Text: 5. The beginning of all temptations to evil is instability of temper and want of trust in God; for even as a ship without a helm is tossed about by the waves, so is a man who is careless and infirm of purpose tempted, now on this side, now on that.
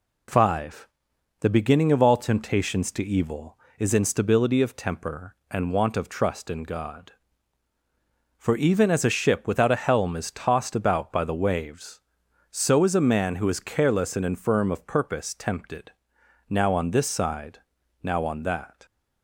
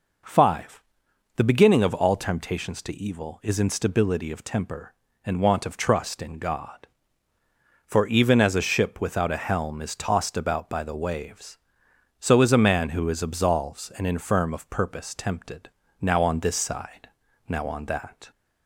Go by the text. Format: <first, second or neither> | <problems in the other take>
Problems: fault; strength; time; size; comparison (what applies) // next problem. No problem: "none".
first | says "absolves" for "careless"; at 13.2 s